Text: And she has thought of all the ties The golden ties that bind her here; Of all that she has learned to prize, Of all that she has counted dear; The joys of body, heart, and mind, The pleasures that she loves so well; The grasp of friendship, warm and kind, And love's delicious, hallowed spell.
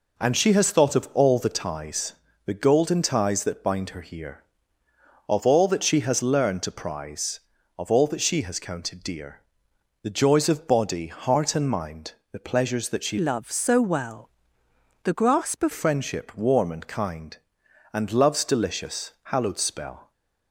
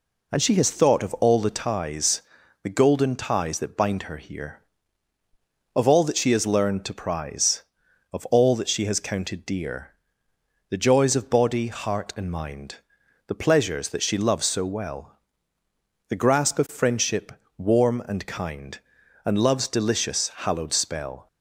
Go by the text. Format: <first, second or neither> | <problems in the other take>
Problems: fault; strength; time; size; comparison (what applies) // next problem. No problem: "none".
second | pauses between "ties" and "The"; slight; at 2.1 s; 0.34 s long; also in the second // changes voice from "loves" to "of"; from 13.1 to 15.7 s; 2.6 s long